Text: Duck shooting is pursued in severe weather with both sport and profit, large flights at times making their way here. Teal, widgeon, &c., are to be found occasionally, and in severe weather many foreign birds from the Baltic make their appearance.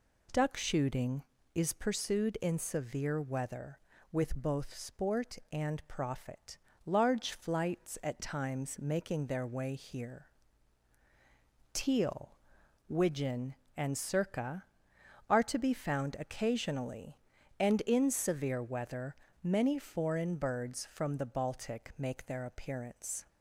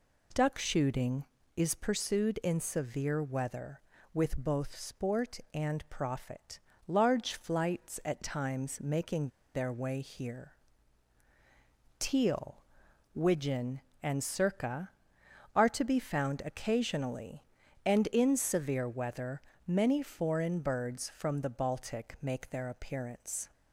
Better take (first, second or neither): first